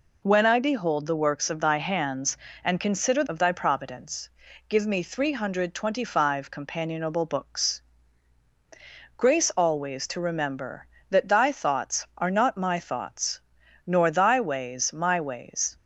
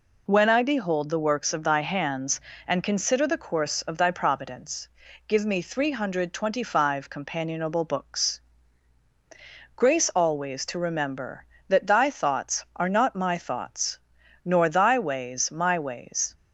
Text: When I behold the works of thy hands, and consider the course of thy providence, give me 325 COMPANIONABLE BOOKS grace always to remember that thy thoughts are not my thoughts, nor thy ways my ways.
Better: second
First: skips "the course"; at 3.2 s // pauses between "BOOKS" and "grace"; strong; at 7.8 s; 1.3 s long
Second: pauses between "BOOKS" and "grace"; strong; at 8.4 s; 1.3 s long

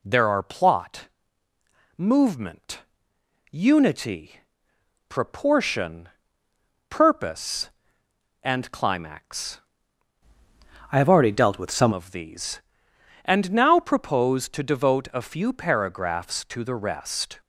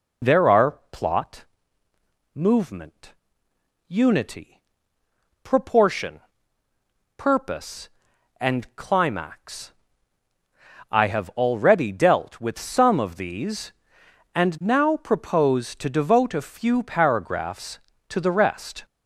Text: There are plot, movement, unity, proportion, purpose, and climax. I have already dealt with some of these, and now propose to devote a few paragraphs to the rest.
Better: second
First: changes voice from "I" to "some"; from 10.9 to 11.9 s; 1.0 s long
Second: none

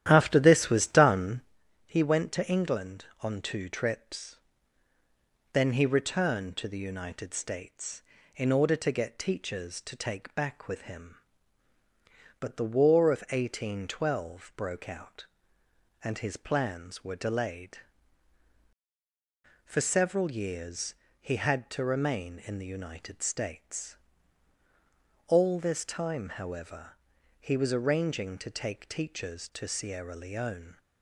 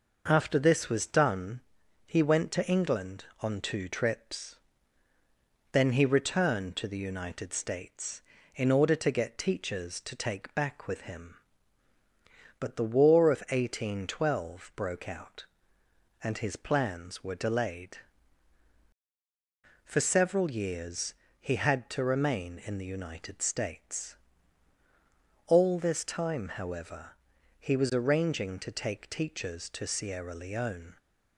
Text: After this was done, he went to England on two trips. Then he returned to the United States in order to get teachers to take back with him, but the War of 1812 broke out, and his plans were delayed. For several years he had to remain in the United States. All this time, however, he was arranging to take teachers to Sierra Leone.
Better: second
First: starts louder than the rest; strong; until 1.6 s; 11.5 dB // pauses between "years" and "he"; slight; at 20.9 s; 0.24 s long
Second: pauses between "years" and "he"; slight; at 21.1 s; 0.24 s long

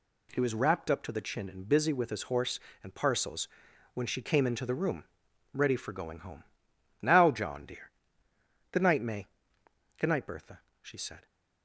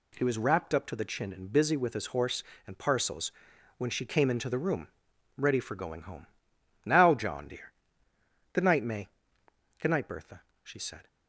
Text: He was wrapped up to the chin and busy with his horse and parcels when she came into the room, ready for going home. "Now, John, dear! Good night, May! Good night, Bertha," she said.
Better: neither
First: pauses between "parcels" and "when"; noticeable; at 3.4 s; 0.46 s long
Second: pauses between "parcels" and "when"; noticeable; at 3.3 s; 0.46 s long

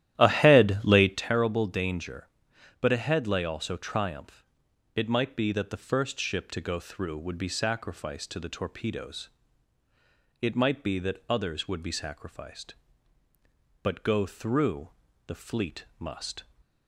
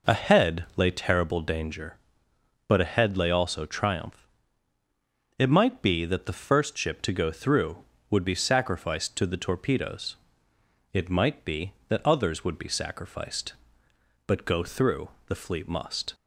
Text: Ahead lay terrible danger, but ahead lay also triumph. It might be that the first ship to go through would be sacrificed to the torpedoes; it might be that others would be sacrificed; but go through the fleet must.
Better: second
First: starts louder than the rest; strong; until 1.3 s; 12.5 dB // pauses between "through" and "the"; slight; at 14.8 s; 0.36 s long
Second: pauses between "through" and "the"; slight; at 15.0 s; 0.20 s long

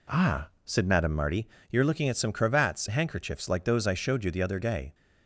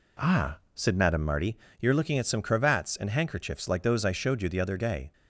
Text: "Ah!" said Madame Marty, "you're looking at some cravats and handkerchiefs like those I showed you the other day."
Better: second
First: skips "and"; at 2.8 s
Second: none

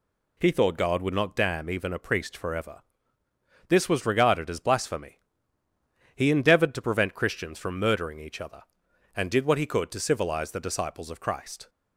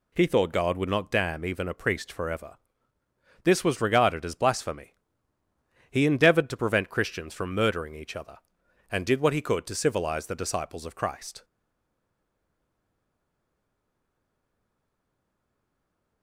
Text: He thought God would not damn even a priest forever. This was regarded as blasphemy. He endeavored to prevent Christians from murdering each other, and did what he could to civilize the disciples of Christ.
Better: first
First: none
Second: stays silent after the last word; strong; from 11.4 s on; 4.8 s long

